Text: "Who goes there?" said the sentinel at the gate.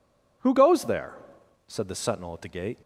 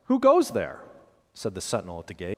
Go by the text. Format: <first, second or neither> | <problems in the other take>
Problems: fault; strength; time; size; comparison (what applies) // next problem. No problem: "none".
first | leaves "gate" unfinished; at 2.3 s; 125 ms